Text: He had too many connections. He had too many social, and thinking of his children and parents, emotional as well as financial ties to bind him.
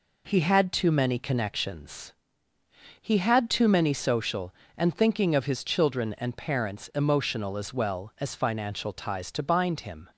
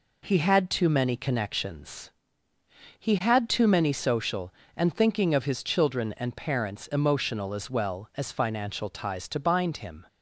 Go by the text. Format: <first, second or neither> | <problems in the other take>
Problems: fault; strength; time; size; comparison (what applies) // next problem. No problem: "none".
neither | none